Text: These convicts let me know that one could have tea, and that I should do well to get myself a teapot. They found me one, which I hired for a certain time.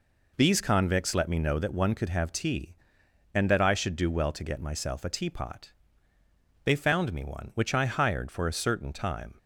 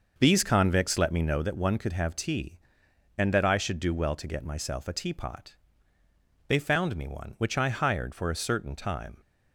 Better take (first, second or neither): first